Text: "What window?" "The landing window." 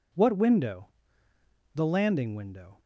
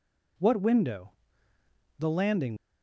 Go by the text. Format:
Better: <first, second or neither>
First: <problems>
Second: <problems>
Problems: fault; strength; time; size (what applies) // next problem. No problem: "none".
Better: first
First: none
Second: stops before "window"; at 2.5 s